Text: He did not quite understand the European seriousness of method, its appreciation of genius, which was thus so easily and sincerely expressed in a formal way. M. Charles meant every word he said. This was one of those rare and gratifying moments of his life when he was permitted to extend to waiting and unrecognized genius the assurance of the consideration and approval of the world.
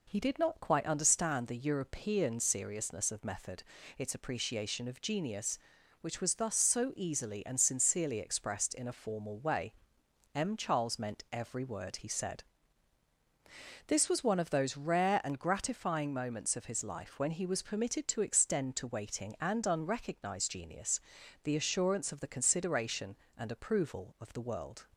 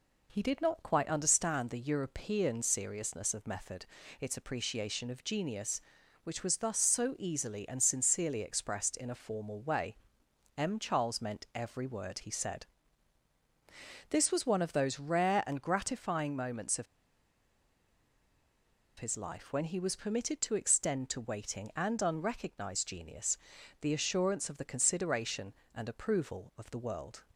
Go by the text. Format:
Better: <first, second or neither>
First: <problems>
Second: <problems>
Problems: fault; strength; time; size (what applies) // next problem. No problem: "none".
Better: first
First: pauses between "genius" and "the"; at 21.0 s; 0.44 s long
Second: pauses between "of" and "his"; strong; at 16.8 s; 2.1 s long // pauses between "genius" and "the"; at 23.3 s; 0.44 s long